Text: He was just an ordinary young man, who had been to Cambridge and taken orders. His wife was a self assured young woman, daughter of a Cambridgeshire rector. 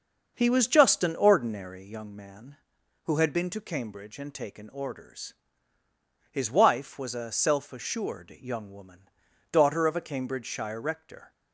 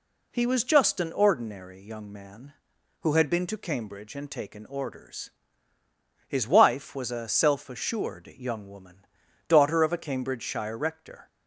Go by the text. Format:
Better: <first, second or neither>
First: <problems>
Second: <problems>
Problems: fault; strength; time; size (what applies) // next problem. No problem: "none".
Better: second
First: starts louder than the rest; until 2.1 s; 6.5 dB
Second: none